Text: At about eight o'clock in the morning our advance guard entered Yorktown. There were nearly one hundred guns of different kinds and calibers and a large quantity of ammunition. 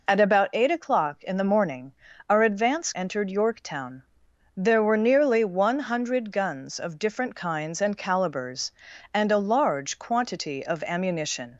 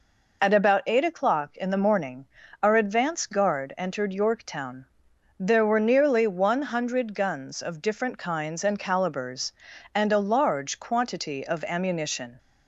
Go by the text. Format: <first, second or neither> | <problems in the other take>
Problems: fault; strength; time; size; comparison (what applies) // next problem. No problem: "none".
second | pauses between "morning" and "our"; at 1.9 s; 0.38 s long; also in the second // skips "guard"; at 2.9 s